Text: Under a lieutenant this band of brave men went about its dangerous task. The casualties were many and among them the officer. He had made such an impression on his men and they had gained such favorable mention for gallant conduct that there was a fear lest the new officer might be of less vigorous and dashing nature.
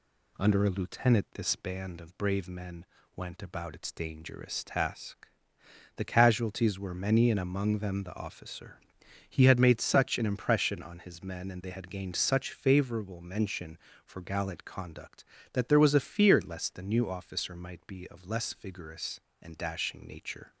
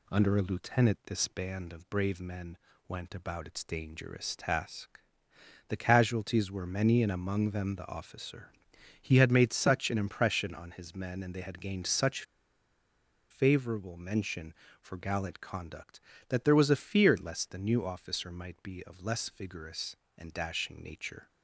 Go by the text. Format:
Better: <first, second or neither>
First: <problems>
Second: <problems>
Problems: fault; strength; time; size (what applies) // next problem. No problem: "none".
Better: first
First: pauses between "men" and "went"; slight; at 2.8 s; 0.30 s long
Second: pauses between "men" and "went"; slight; at 2.5 s; 0.30 s long // pauses between "such" and "favorable"; at 12.2 s; 1.0 s long